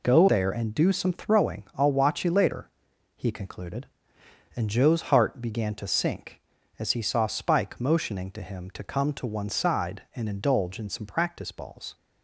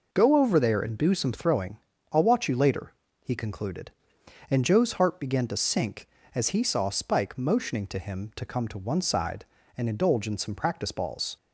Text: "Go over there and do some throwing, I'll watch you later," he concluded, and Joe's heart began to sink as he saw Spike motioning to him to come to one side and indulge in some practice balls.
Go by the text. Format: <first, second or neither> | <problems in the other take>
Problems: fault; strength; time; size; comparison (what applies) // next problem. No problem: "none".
second | skips "over"; at 0.2 s